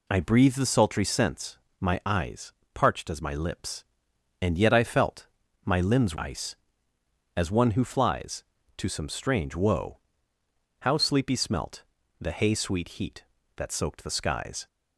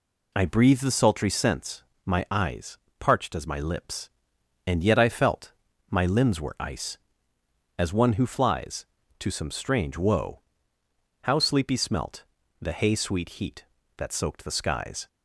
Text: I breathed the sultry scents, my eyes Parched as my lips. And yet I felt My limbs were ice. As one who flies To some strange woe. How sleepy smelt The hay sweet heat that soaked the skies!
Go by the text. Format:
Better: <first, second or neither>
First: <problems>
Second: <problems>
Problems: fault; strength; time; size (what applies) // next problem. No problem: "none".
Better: second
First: pauses between "eyes" and "Parched"; slight; at 2.5 s; 0.24 s long // pauses between "felt" and "My"; slight; at 5.2 s; 0.36 s long // skips "were"; at 6.1 s // pauses between "smelt" and "The"; at 11.8 s; 0.38 s long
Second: pauses between "eyes" and "Parched"; slight; at 2.7 s; 0.24 s long // pauses between "felt" and "My"; slight; at 5.5 s; 0.36 s long // pauses between "smelt" and "The"; at 12.2 s; 0.38 s long